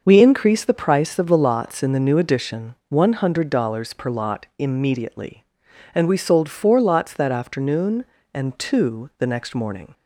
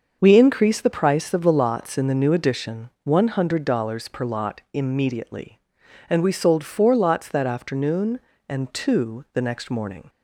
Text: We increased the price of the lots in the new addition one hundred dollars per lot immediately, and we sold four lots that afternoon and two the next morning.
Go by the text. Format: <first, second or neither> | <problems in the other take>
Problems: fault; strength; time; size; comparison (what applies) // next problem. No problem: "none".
neither | starts louder than the rest; the same in both